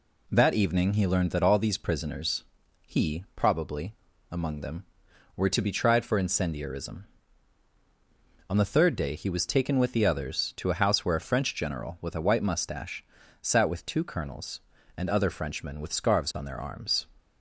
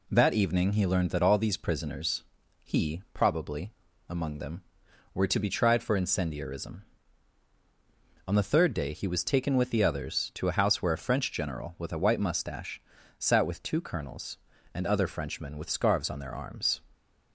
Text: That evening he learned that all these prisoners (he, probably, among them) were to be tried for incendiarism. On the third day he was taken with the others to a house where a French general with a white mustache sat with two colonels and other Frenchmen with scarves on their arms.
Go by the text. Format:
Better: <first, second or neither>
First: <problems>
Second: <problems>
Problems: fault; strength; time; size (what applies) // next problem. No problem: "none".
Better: neither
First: pauses between "mustache" and "sat"; slight; at 13.0 s; 0.36 s long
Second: pauses between "mustache" and "sat"; slight; at 12.8 s; 0.36 s long